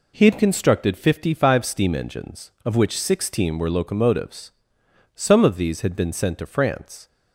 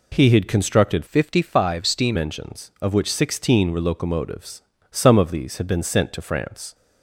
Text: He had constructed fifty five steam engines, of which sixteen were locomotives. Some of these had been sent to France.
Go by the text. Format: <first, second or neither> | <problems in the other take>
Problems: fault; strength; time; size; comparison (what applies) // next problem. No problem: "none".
first | changes voice from "fifty" to "steam"; from 1.0 to 2.1 s; 1.1 s long